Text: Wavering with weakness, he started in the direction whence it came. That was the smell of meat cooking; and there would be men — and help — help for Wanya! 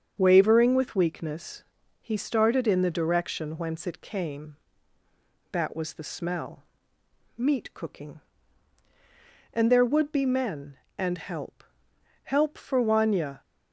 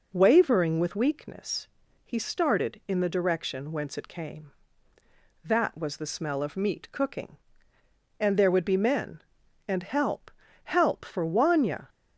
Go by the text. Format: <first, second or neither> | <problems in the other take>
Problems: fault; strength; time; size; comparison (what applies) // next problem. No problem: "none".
second | starts louder than the rest; strong; until 1.1 s; 7 dB // skips "of"; at 6.9 s